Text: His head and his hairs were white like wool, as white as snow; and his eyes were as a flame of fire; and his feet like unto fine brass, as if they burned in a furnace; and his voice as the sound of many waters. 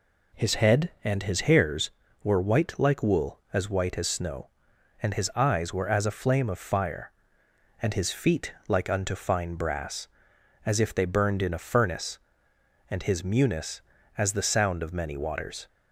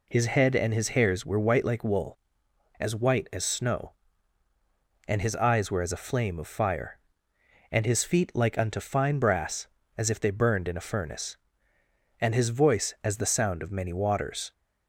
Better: second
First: pauses between "feet" and "like"; slight; at 8.5 s; 0.16 s long // says "munis" for "voice"; at 13.2 s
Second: none

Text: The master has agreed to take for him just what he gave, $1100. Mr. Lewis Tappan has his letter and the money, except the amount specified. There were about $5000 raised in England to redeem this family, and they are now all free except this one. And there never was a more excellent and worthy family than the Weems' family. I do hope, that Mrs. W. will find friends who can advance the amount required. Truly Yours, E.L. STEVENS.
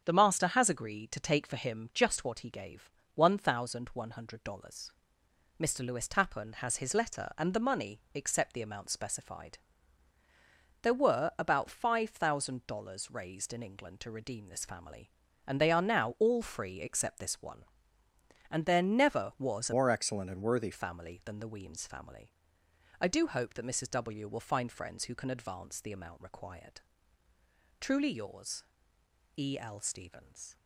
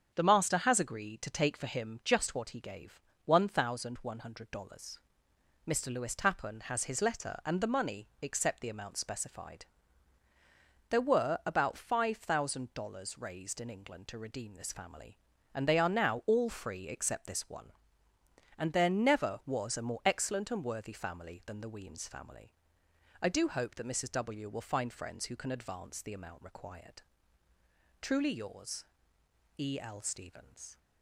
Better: second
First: starts louder than the rest; strong; until 1.0 s; 7.5 dB // changes voice from "more" to "worthy"; from 19.7 to 20.7 s; 1.0 s long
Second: starts louder than the rest; strong; until 1.1 s; 7.5 dB

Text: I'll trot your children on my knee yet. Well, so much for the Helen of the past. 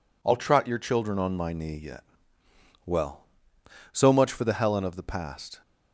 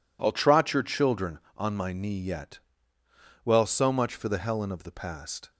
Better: neither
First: none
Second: none

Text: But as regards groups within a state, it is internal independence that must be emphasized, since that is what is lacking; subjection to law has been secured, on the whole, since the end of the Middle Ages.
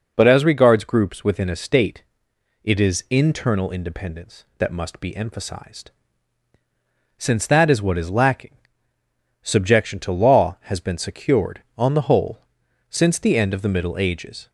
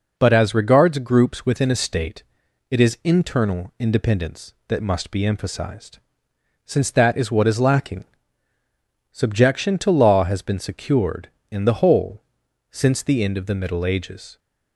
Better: first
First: none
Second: says "in" for "on"; at 11.5 s

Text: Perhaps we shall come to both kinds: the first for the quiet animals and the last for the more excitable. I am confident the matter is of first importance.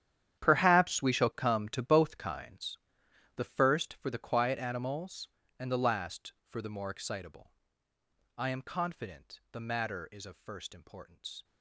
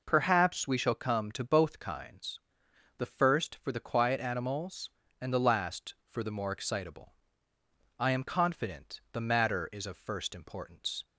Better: second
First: gets quieter; strong; throughout; 16.5 dB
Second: none

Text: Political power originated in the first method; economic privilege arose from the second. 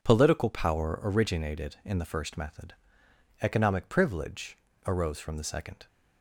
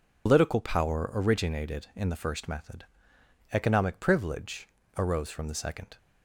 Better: first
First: pauses between "privilege" and "arose"; slight; at 4.5 s; 0.30 s long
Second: loses the start of "Political"; at 0.2 s; 120 ms // pauses between "privilege" and "arose"; slight; at 4.6 s; 0.30 s long

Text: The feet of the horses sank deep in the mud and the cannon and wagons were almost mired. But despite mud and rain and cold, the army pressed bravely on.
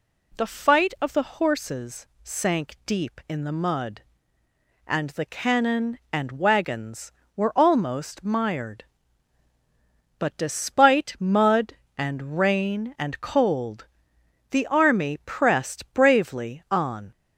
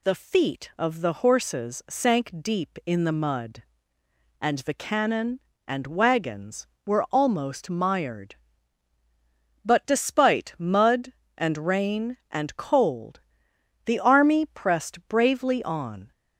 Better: second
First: says "fight" for "feet"; at 0.4 s // pauses between "horses" and "sank"; slight; at 2.0 s; 0.16 s long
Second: none

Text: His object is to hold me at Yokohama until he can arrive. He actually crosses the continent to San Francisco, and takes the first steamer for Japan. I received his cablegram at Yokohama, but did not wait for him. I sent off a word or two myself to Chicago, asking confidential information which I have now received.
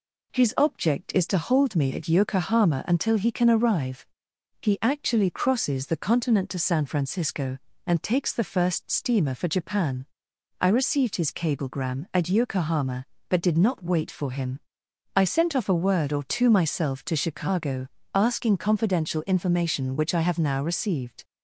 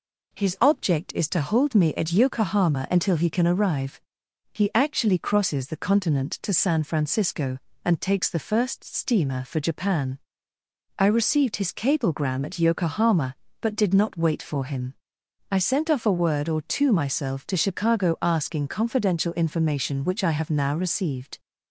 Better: neither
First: none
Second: none

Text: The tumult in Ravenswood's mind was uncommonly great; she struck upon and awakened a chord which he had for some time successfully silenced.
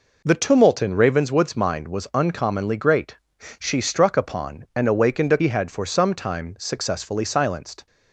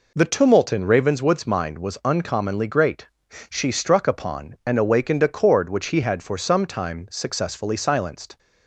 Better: second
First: skips "chord which"; at 5.3 s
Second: none

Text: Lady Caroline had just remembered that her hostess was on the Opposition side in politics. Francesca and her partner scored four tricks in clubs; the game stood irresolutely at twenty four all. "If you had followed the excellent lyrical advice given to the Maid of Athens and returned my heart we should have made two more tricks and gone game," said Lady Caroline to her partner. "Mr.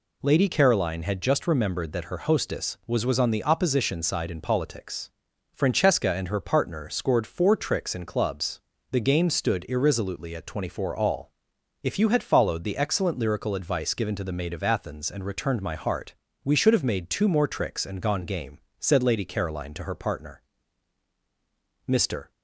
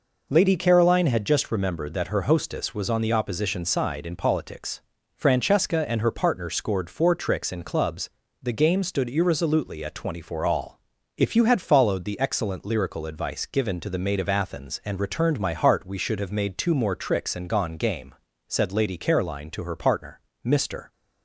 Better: second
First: says "was" twice; at 3.0 s // pauses between "heart" and "we"; slight; at 16.1 s; 0.32 s long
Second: none

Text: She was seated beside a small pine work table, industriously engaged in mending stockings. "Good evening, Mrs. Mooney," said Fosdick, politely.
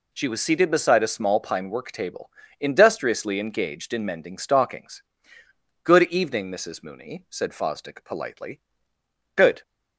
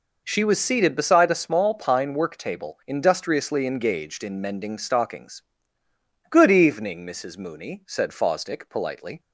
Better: second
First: goes on to say "Good"; slight; from 9.3 s on; 0.26 s long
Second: none

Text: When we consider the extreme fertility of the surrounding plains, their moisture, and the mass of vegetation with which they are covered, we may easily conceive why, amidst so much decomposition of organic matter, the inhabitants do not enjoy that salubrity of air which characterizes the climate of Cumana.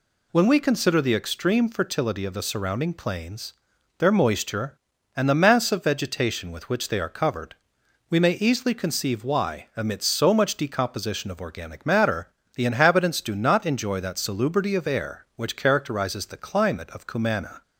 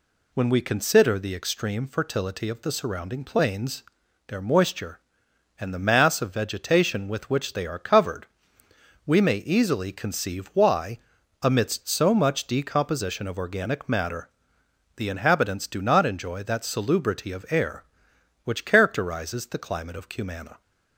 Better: neither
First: none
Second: none

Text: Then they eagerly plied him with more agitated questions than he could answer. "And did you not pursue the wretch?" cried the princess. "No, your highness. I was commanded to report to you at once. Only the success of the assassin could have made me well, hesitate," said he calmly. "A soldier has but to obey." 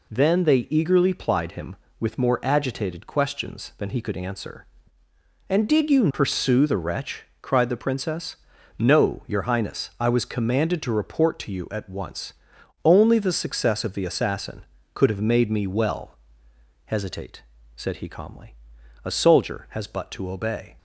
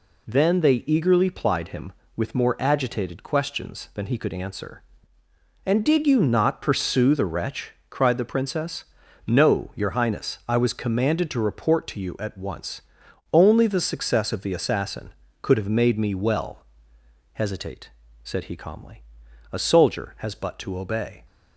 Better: second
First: skips "not"; at 6.1 s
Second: none

